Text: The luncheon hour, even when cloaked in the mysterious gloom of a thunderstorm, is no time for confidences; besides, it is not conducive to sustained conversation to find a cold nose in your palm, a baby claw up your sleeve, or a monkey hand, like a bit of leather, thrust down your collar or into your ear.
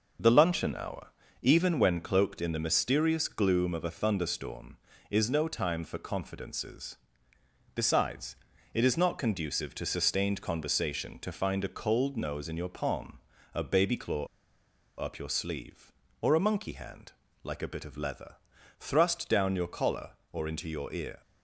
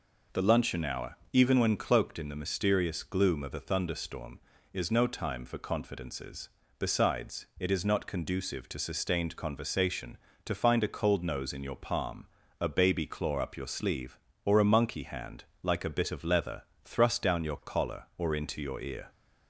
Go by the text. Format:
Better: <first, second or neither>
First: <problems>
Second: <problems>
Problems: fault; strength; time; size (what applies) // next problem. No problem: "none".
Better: second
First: pauses between "claw" and "up"; noticeable; at 14.2 s; 0.73 s long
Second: none